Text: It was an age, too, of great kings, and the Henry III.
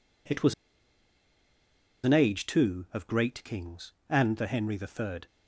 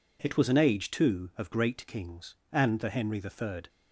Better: second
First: pauses between "was" and "an"; strong; at 0.5 s; 1.5 s long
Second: none

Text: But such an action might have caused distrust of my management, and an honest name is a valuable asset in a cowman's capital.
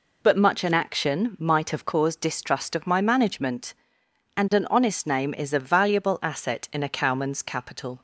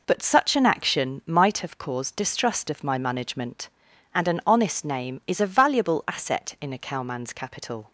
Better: second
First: says "much" for "such"; at 0.3 s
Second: none

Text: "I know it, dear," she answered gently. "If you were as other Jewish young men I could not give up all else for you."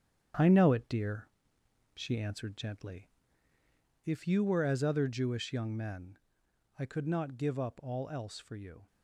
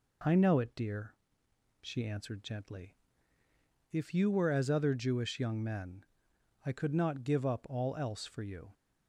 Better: second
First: gets quieter; noticeable; throughout; 6 dB // pauses between "men" and "I"; noticeable; at 6.1 s; 0.60 s long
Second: pauses between "men" and "I"; noticeable; at 6.0 s; 0.60 s long

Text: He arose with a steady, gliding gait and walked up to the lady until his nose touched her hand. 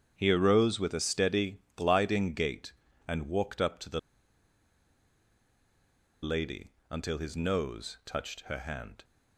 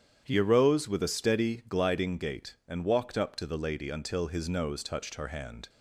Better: second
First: starts louder than the rest; strong; until 1.1 s; 8.5 dB // pauses between "the" and "lady"; strong; at 3.9 s; 2.2 s long // pauses between "lady" and "until"; slight; at 6.7 s; 0.18 s long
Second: starts louder than the rest; strong; until 1.2 s; 8.5 dB

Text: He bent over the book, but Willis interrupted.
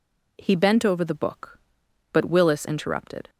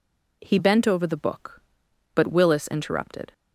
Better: neither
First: none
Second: none

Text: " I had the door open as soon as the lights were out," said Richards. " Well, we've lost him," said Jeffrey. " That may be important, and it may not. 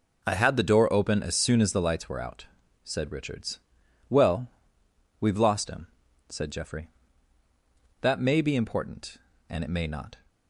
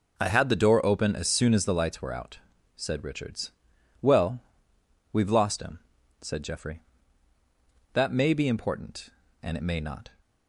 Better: neither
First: none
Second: none

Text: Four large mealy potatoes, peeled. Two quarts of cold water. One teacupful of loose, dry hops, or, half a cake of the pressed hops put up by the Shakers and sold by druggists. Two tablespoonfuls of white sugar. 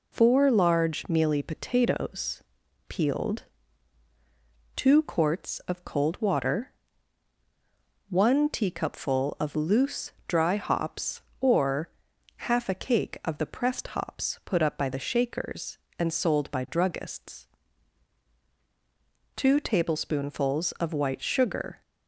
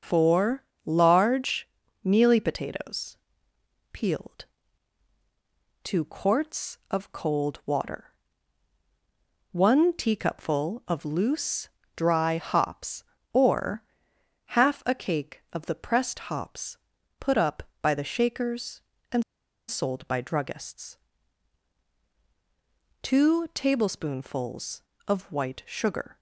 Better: first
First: none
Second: starts louder than the rest; noticeable; until 1.2 s; 6 dB // pauses between "Four" and "large"; slight; at 0.6 s; 0.18 s long // pauses between "large" and "mealy"; at 1.6 s; 0.38 s long // pauses between "hops" and "put"; at 16.7 s; 0.42 s long // pauses between "and" and "sold"; at 19.2 s; 0.45 s long

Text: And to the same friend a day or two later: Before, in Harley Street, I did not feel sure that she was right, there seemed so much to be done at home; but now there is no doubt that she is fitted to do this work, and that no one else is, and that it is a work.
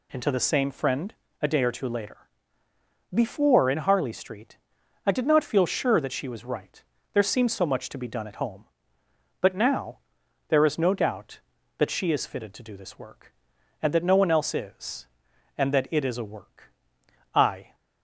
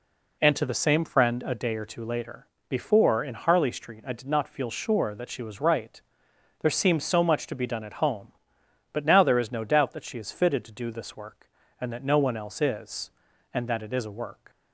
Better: second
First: pauses between "friend" and "a"; slight; at 1.1 s; 0.28 s long // pauses between "now" and "there"; noticeable; at 9.9 s; 0.50 s long // goes on to say "I"; slight; from 17.3 s on; 0.42 s long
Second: none

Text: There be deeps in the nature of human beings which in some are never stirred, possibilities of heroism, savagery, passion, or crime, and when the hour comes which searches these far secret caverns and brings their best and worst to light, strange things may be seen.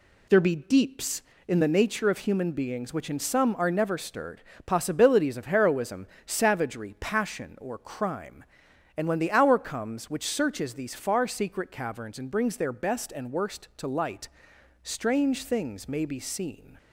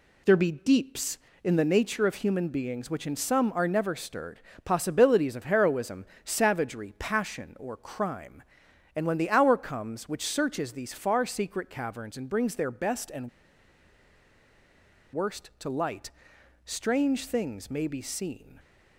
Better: first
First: none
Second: pauses between "and" and "worst"; strong; at 13.2 s; 1.8 s long

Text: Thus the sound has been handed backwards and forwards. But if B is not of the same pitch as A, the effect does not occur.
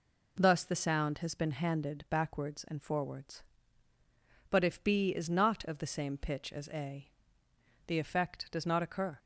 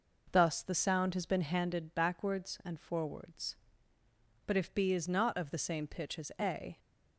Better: first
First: none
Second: stops before "the effect does not occur"; at 6.7 s

